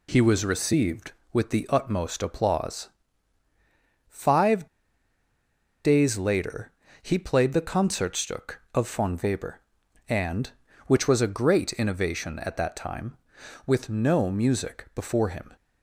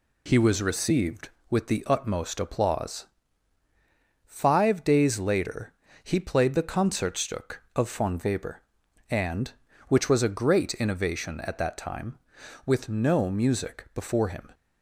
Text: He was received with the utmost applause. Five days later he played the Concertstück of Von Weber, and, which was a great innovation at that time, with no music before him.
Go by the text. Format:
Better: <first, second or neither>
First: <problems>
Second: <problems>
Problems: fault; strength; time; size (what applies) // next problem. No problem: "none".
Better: second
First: pauses between "Five" and "days"; at 4.6 s; 1.1 s long // pauses between "later" and "he"; slight; at 6.7 s; 0.30 s long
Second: pauses between "later" and "he"; slight; at 5.7 s; 0.30 s long